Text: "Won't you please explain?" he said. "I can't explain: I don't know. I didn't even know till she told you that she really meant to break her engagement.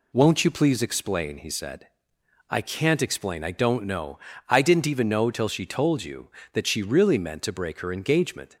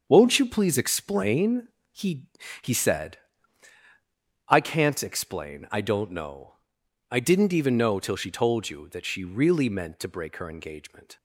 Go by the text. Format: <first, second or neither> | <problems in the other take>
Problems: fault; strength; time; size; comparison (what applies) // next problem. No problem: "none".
first | starts louder than the rest; until 1.0 s; 7 dB // says "he" twice; at 2.6 s